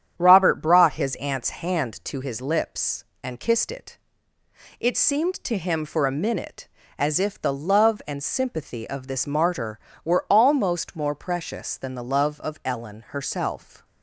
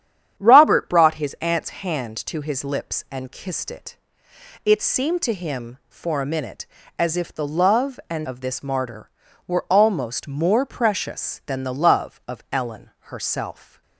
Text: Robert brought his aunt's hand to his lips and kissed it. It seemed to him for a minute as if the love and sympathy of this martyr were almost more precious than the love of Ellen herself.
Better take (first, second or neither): first